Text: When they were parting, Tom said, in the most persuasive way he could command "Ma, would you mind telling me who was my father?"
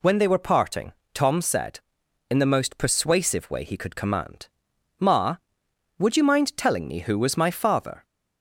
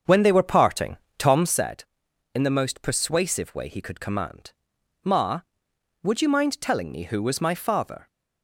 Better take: first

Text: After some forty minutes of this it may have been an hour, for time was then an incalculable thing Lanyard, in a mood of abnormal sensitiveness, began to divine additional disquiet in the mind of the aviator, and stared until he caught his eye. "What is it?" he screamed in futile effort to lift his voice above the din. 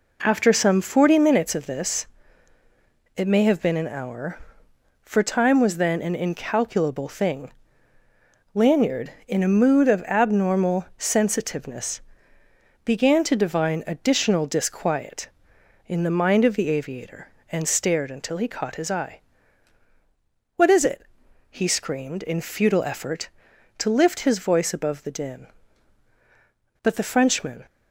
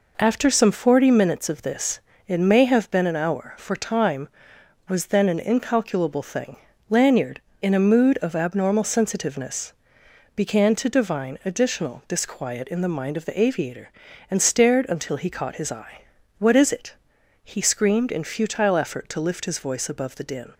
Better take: second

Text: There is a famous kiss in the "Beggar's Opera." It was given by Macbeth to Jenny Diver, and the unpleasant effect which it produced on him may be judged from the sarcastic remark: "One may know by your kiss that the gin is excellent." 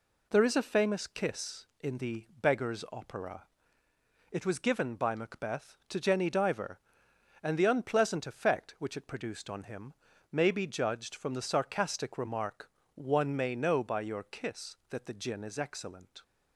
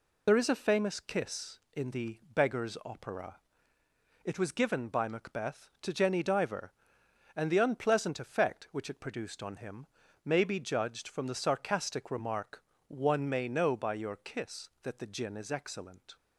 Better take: first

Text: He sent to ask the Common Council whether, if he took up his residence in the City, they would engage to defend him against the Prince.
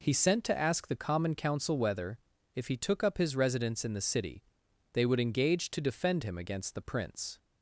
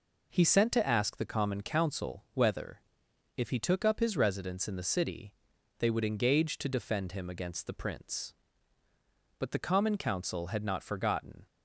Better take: first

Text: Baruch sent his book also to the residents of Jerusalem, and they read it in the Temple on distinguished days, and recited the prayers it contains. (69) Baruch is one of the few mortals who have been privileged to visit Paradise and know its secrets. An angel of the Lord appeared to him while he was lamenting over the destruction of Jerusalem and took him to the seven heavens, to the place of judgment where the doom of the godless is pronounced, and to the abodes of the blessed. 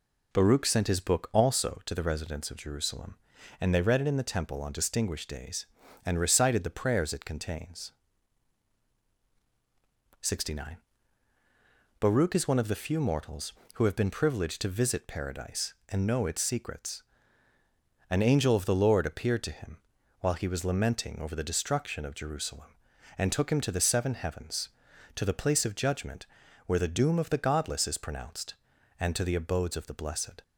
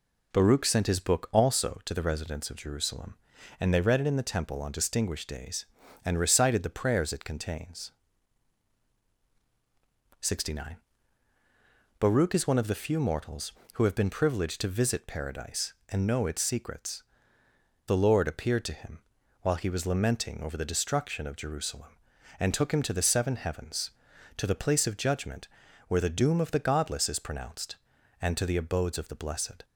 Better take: first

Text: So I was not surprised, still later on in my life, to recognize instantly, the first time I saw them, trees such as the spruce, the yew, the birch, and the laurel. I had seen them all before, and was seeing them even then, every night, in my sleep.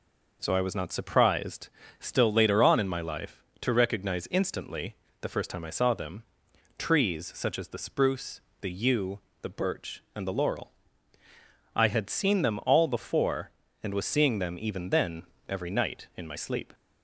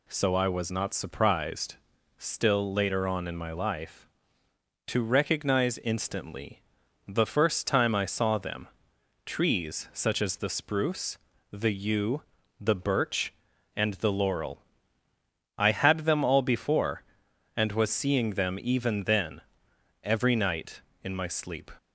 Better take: first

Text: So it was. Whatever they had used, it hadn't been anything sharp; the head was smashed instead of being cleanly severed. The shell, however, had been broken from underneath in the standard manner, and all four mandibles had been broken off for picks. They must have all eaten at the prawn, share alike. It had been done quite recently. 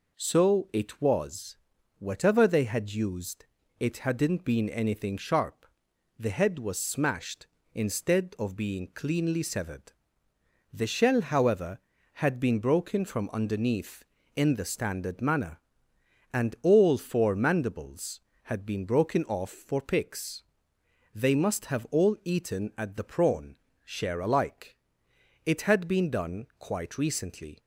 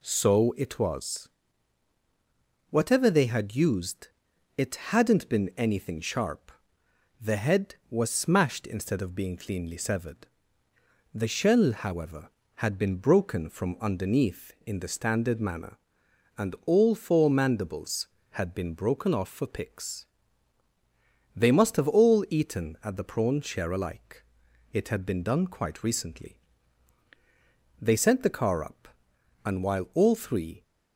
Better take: first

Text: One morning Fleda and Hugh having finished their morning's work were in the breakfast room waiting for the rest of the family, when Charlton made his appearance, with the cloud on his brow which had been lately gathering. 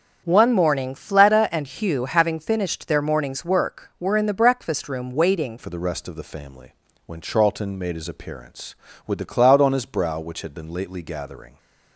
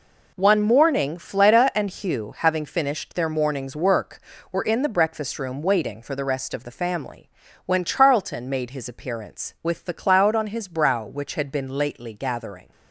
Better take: second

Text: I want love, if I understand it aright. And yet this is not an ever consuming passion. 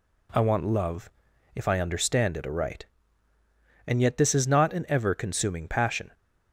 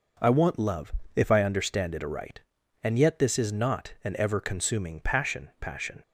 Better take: first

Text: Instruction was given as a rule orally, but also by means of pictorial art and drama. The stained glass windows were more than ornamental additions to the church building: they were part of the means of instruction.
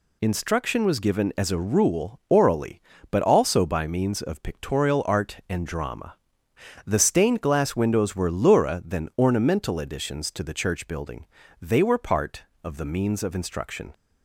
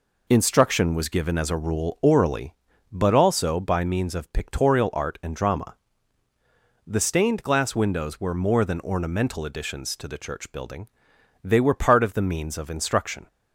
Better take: second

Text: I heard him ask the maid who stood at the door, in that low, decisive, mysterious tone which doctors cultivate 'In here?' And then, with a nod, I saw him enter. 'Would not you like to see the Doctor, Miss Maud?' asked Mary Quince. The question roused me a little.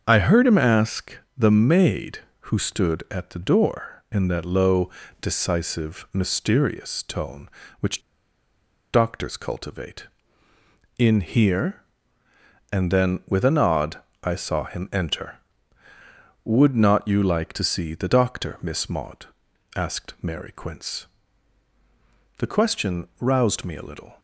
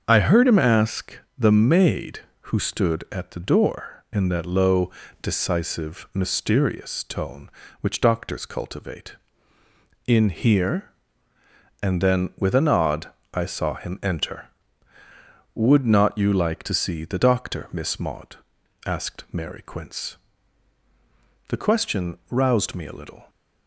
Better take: second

